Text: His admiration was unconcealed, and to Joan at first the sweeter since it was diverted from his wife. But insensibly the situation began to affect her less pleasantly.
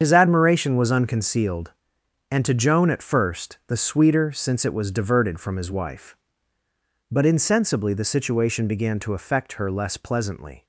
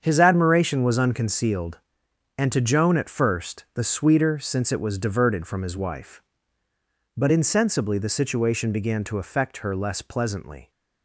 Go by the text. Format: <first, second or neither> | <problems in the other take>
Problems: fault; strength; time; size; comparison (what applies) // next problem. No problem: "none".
second | loses the start of "His"; at 0.0 s; 55 ms // starts louder than the rest; strong; until 1.0 s; 7.5 dB; strong in the second